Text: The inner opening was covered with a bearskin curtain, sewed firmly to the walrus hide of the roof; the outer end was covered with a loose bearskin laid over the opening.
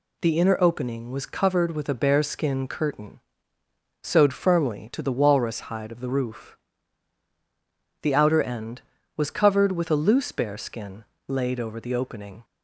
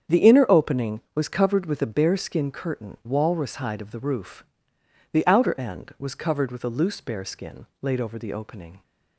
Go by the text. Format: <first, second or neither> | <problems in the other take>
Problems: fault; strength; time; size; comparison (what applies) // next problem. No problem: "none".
first | starts louder than the rest; strong; until 1.2 s; 8 dB // skips "sewed firmly to the"; at 3.0 s // pauses between "bearskin" and "laid"; slight; at 7.6 s; 0.16 s long; slight in the first